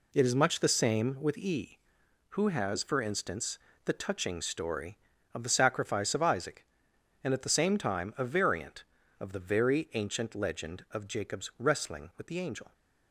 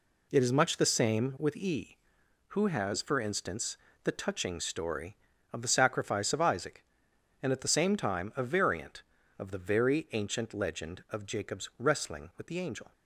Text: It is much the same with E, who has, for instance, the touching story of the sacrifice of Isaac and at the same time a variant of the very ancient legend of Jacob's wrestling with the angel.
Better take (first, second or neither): neither